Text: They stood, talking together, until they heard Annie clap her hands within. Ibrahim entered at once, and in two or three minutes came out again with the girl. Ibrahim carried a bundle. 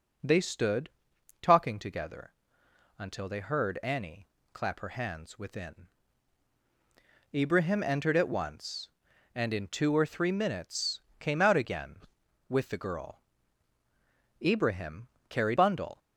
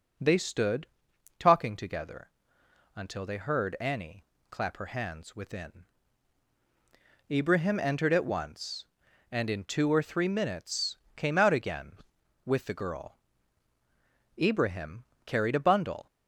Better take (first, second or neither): second